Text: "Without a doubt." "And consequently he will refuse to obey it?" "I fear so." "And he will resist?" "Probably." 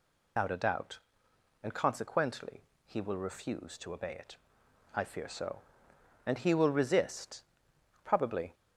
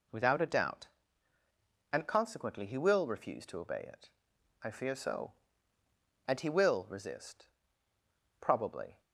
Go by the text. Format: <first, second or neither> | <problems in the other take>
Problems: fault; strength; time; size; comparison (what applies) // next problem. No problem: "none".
second | loses the start of "Without"; at 0.3 s; 145 ms // pauses between "consequently" and "he"; slight; at 2.6 s; 0.22 s long